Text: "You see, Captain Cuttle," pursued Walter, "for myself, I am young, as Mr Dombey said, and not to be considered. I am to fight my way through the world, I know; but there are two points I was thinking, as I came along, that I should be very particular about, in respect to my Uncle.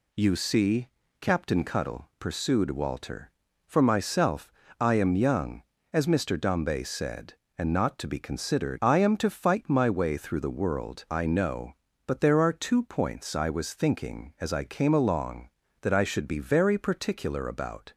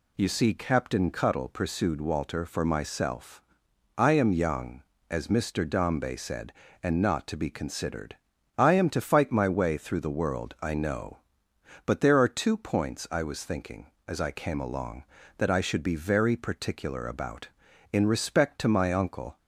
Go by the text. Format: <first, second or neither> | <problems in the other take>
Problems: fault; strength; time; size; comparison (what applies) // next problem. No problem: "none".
second | stops before "in respect to my Uncle"; at 17.9 s